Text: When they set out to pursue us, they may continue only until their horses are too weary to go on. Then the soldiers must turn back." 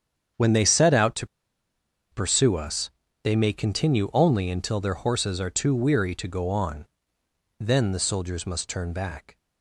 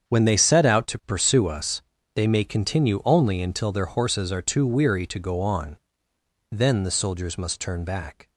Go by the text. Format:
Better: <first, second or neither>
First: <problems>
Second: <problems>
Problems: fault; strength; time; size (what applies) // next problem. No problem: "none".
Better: second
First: starts louder than the rest; strong; until 2.2 s; 7.5 dB // pauses between "to" and "pursue"; noticeable; at 1.2 s; 0.83 s long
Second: starts louder than the rest; strong; until 1.1 s; 7.5 dB